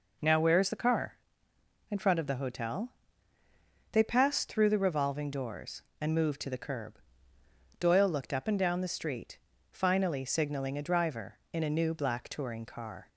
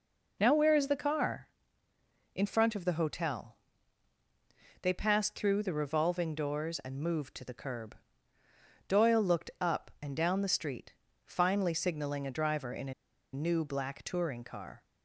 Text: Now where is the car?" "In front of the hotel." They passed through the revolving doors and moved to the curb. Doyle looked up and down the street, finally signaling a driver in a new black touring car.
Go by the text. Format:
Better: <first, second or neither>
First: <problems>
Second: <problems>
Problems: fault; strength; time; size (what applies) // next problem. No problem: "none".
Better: first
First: none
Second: pauses between "a" and "new"; at 12.9 s; 0.40 s long